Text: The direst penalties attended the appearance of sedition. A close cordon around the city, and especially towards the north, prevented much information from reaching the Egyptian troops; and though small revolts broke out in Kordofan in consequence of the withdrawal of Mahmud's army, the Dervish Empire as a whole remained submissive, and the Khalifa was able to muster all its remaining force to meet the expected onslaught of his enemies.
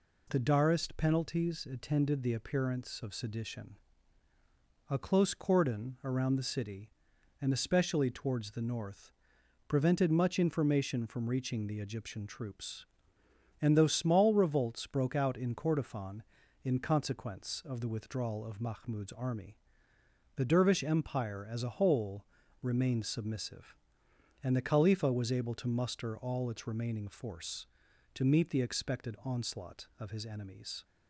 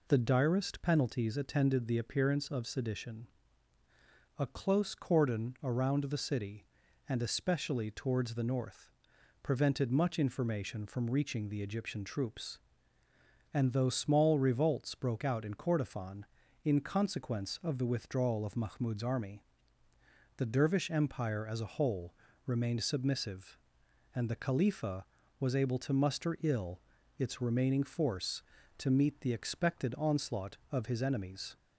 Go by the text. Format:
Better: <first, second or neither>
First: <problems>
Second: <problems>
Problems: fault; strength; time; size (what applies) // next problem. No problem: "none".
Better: first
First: pauses between "whole" and "remained"; slight; at 22.2 s; 0.34 s long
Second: pauses between "whole" and "remained"; slight; at 22.1 s; 0.30 s long // says "ill" for "all"; at 26.4 s